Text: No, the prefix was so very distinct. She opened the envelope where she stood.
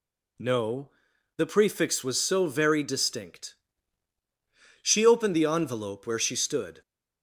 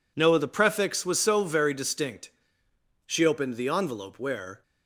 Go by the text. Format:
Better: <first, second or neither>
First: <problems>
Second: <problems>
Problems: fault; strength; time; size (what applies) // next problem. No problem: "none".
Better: first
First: none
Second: stops before "she stood"; at 4.6 s